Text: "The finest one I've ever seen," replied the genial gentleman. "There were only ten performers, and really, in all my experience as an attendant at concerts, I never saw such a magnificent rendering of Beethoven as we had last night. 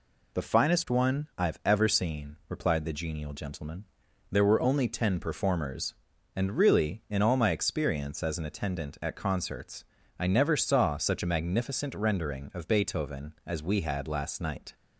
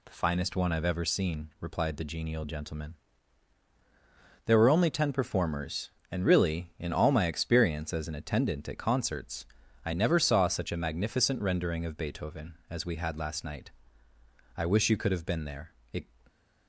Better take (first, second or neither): first